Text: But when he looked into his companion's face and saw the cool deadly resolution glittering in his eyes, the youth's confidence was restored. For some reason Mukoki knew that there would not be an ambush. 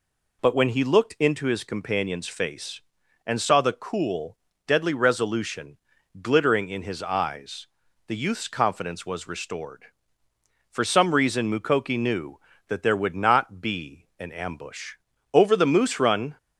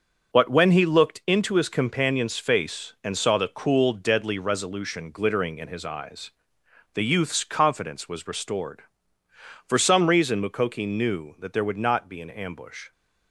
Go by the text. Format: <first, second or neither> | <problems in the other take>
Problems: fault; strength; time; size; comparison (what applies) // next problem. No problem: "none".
second | pauses between "cool" and "deadly"; slight; at 4.3 s; 0.30 s long // pauses between "resolution" and "glittering"; at 5.7 s; 0.44 s long // goes on to say "Over the moose run"; noticeable; from 15.3 s on; 1.0 s long